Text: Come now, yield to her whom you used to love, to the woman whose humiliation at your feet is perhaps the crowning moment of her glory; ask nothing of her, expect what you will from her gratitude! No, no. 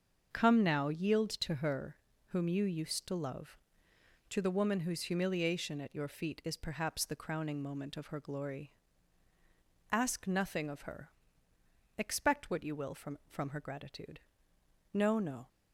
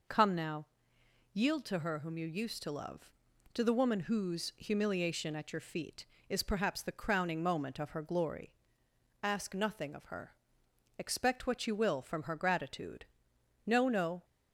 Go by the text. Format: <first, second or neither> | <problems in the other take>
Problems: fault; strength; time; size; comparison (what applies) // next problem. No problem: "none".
second | starts louder than the rest; until 1.3 s; 6.5 dB // pauses between "her" and "whom"; slight; at 1.9 s; 0.32 s long // says "from" twice; at 13.2 s